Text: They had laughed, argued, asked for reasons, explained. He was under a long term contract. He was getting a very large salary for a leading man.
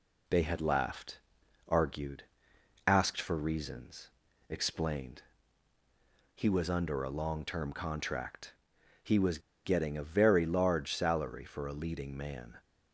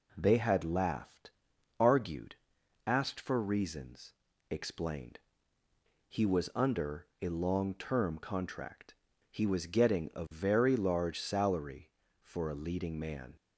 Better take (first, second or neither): second